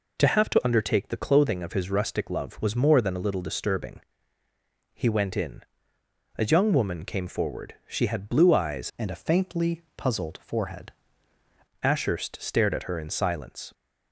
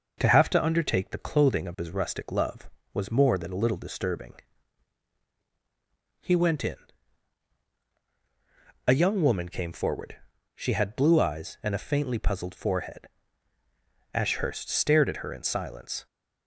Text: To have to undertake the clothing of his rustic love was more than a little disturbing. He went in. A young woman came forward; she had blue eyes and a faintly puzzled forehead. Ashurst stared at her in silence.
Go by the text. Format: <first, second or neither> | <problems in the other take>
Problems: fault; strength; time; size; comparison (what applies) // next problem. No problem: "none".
second | changes voice from "and" to "forehead"; from 8.9 to 10.8 s; 1.9 s long